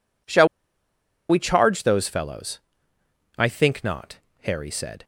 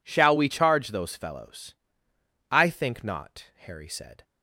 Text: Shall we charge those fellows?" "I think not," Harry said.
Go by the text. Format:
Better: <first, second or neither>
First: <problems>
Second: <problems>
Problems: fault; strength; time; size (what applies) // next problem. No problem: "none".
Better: second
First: pauses between "Shall" and "we"; noticeable; at 0.4 s; 0.82 s long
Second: none